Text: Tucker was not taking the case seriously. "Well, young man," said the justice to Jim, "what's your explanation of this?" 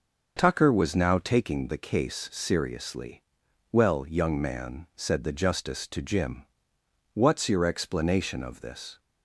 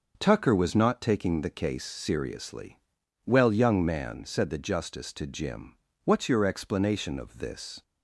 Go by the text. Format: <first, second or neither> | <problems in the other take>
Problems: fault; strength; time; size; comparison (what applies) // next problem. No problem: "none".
second | starts louder than the rest; until 1.3 s; 6 dB // says "now" for "not"; at 0.9 s